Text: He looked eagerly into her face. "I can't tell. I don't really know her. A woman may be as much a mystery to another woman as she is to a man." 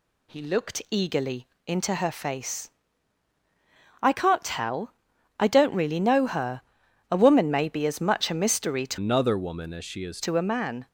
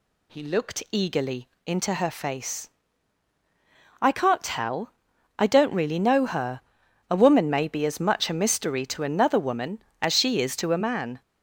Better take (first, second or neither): second